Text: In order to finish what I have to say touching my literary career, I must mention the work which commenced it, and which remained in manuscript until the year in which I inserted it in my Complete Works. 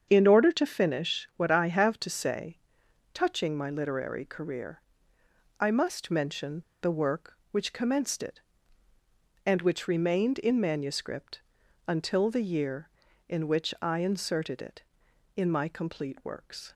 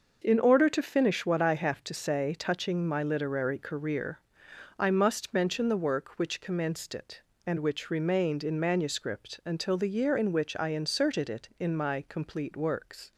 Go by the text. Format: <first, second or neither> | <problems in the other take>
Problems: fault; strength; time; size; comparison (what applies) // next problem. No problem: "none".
second | starts louder than the rest; strong; until 1.0 s; 7.5 dB; noticeable in the second // pauses between "say" and "touching"; noticeable; at 2.5 s; 0.56 s long // pauses between "mention" and "the"; slight; at 6.6 s; 0.19 s long // pauses between "manuscript" and "until"; noticeable; at 11.4 s; 0.46 s long